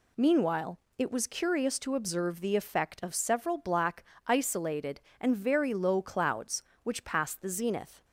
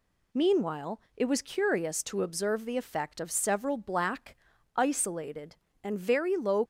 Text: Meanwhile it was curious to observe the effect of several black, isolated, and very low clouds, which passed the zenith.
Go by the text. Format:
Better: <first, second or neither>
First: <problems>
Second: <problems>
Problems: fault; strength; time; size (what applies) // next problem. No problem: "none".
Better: first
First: pauses between "Meanwhile" and "it"; slight; at 0.7 s; 0.18 s long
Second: pauses between "Meanwhile" and "it"; slight; at 0.9 s; 0.16 s long // stops before "clouds which passed the zenith"; at 6.6 s